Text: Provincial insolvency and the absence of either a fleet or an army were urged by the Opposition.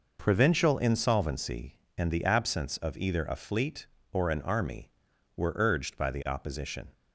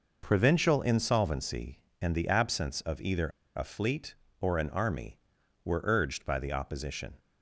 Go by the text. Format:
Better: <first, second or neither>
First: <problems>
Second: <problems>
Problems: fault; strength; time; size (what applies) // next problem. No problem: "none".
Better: first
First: none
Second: pauses between "either" and "a"; slight; at 3.2 s; 0.27 s long